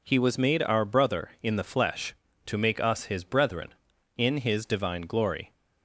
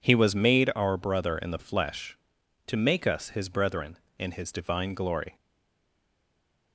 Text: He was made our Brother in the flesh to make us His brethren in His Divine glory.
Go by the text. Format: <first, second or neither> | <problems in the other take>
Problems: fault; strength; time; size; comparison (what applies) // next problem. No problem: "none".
first | stays silent after the last word; noticeable; from 5.3 s on; 1.4 s long